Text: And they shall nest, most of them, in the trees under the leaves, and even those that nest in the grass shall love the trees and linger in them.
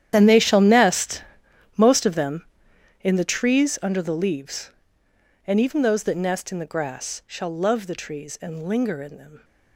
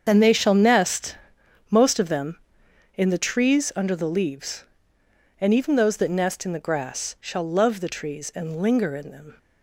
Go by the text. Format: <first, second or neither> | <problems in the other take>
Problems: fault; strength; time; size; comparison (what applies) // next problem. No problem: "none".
second | gets quieter; strong; throughout; 17 dB // starts louder than the rest; strong; until 1.1 s; 10.5 dB; strong in the second